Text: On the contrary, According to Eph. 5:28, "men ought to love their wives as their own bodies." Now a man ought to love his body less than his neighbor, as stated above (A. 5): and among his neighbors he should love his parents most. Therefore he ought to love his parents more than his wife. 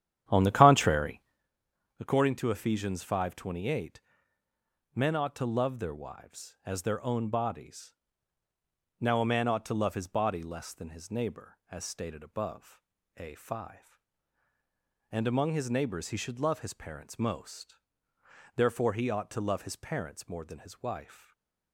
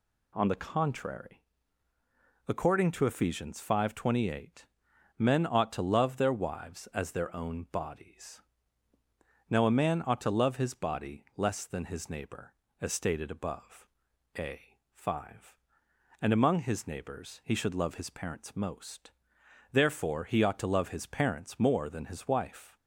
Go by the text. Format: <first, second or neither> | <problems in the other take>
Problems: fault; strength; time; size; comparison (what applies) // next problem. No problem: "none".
second | starts louder than the rest; strong; until 1.5 s; 10 dB // stays silent after the last word; slight; from 21.1 s on; 0.6 s long